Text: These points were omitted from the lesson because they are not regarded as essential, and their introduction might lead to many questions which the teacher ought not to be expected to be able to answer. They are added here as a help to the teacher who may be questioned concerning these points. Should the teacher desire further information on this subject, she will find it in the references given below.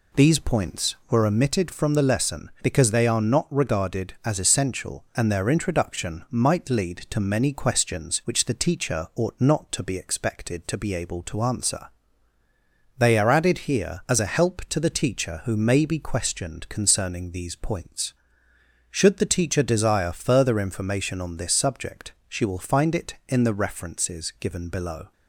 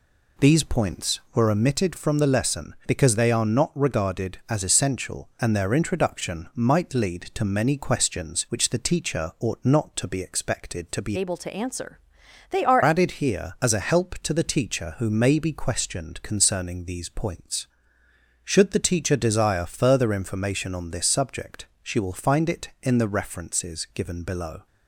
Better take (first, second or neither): first